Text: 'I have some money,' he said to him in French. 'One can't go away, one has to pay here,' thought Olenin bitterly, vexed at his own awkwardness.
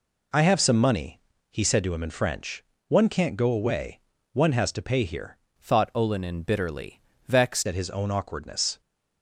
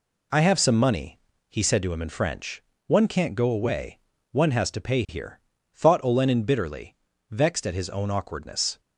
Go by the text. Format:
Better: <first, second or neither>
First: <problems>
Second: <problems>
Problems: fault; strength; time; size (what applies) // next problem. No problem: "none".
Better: second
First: changes voice from "thought" to "vexed"; from 5.6 to 7.6 s; 2.0 s long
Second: none